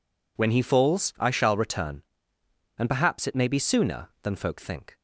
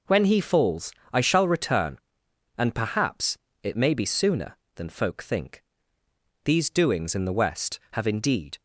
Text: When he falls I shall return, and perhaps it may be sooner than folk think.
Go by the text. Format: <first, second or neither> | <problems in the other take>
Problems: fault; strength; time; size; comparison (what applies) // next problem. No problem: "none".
first | pauses between "falls" and "I"; slight; at 0.9 s; 0.20 s long // pauses between "perhaps" and "it"; slight; at 3.3 s; 0.26 s long // goes on to say "These doings in the West have indeed"; strong; from 6.4 s on; 2.1 s long